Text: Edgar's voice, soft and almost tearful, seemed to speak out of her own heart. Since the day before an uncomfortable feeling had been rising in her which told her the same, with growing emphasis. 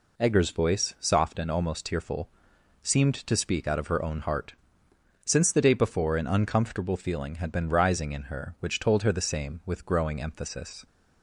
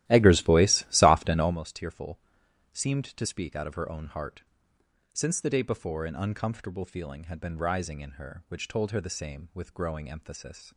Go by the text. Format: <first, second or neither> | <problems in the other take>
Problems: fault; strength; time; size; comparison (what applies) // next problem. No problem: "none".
first | starts louder than the rest; strong; until 1.6 s; 14.5 dB